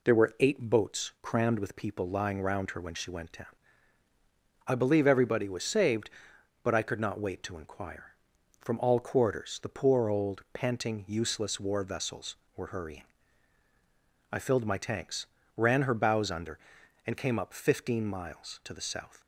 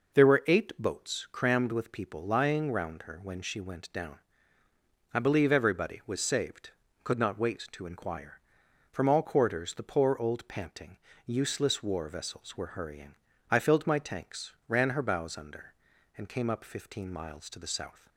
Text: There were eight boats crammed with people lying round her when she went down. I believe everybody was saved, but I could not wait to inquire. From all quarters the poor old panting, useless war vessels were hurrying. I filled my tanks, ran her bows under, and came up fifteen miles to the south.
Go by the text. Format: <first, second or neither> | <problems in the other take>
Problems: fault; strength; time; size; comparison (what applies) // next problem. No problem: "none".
first | skips "but I"; at 6.8 s